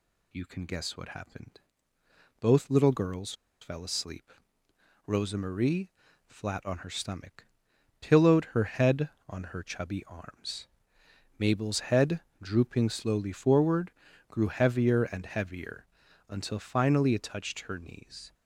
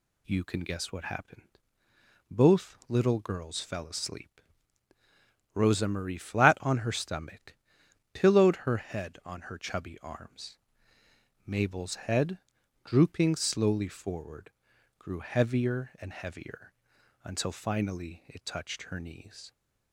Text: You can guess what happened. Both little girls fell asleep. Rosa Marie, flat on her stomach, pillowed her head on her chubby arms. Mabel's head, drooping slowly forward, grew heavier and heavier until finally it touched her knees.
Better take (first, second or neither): second